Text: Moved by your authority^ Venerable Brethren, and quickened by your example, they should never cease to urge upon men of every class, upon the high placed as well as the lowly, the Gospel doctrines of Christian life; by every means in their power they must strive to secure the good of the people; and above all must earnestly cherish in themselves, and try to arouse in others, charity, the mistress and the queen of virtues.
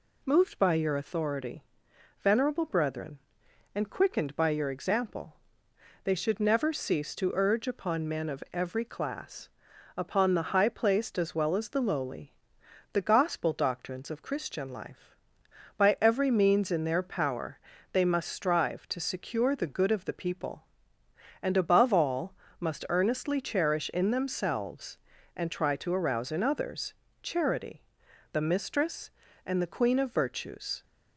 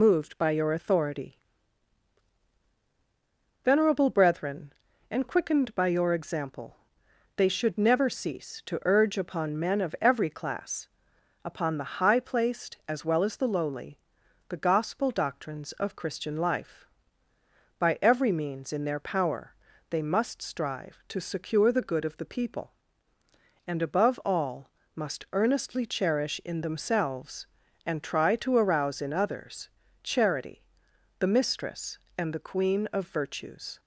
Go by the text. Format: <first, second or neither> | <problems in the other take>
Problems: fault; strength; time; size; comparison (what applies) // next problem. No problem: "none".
first | loses the start of "Moved"; at 0.0 s; 40 ms // pauses between "authority" and "Venerable"; strong; at 1.3 s; 2.2 s long; noticeable in the first // pauses between "power" and "they"; at 19.5 s; 0.38 s long; slight in the first // pauses between "all" and "must"; slight; at 24.6 s; 0.24 s long; slight in the first